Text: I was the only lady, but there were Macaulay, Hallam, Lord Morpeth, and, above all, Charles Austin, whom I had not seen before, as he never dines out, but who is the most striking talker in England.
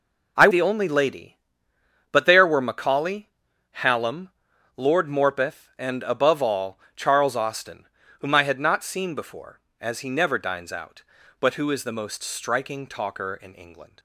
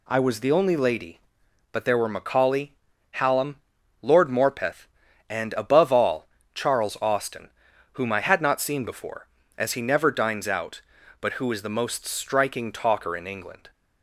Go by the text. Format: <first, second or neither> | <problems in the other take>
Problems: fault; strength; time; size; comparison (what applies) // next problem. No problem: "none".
second | skips "was"; at 0.4 s